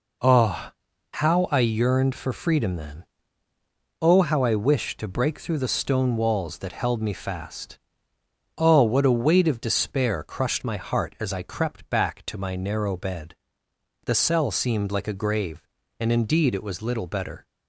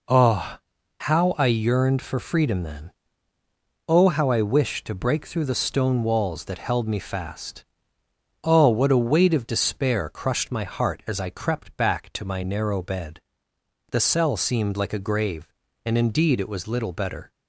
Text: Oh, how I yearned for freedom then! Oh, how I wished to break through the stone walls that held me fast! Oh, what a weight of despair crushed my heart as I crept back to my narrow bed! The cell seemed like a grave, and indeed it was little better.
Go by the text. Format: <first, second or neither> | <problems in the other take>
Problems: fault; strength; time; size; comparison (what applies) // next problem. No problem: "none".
neither | none